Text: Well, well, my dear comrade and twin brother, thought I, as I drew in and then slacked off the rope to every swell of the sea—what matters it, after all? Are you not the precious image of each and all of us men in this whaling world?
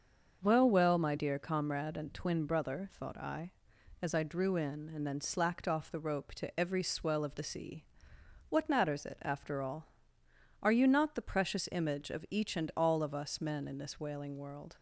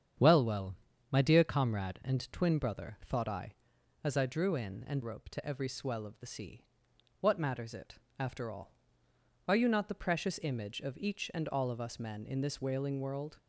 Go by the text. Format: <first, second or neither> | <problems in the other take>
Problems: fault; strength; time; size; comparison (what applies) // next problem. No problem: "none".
first | starts louder than the rest; strong; until 1.5 s; 8 dB; noticeable in the first // skips "then slacked off the"; at 5.0 s